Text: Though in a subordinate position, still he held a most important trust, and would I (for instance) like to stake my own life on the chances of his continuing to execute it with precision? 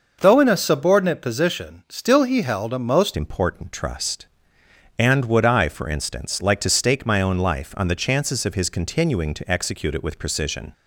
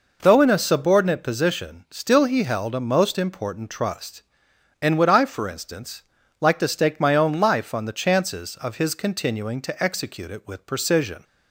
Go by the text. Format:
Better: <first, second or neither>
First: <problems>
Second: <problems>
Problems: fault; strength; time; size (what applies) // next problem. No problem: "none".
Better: second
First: changes voice at "important"; from 3.1 s on; 7.6 s long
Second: none